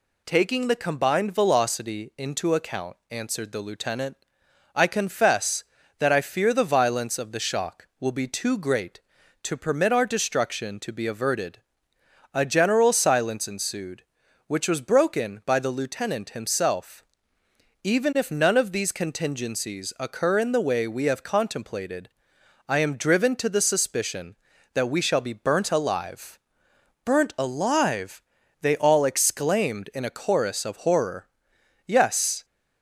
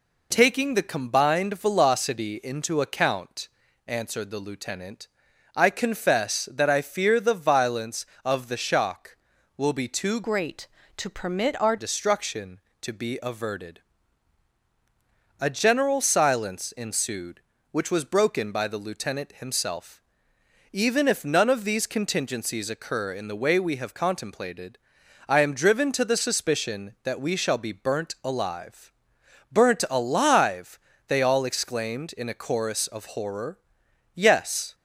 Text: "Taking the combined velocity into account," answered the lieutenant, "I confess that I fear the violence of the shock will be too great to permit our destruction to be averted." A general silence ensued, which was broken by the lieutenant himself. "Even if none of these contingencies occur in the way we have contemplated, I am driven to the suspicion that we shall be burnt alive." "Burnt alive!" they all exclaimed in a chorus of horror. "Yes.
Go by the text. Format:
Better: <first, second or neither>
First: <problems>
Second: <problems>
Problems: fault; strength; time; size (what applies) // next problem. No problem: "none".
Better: first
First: none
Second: changes voice from "great" to "our"; from 10.2 to 11.7 s; 1.5 s long